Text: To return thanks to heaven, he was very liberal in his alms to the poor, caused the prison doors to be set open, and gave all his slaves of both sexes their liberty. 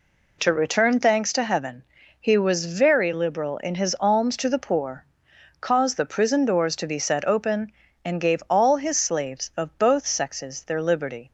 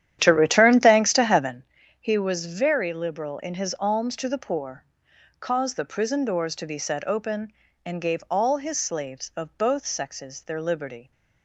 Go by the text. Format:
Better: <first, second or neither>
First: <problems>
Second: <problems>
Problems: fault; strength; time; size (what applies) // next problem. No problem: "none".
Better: first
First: none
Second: starts louder than the rest; strong; until 1.7 s; 10.5 dB